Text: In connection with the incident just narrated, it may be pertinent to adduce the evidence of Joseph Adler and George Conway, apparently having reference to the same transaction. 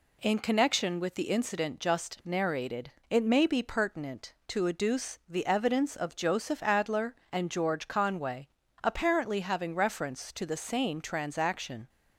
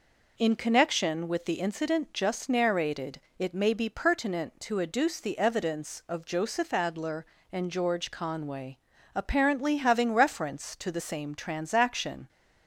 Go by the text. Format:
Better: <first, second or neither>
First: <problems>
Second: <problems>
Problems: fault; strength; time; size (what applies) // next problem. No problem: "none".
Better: neither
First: none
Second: none